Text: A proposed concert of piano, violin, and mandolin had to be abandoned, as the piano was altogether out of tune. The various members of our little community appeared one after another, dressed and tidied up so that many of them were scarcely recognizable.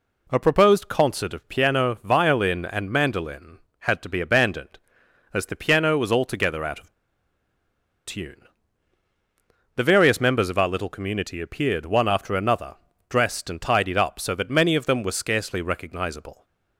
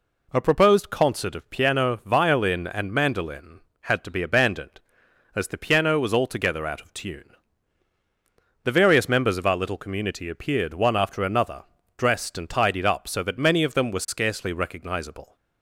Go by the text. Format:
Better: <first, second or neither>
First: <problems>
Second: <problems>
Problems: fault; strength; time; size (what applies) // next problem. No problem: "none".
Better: second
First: pauses between "of" and "tune"; at 6.9 s; 1.1 s long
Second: none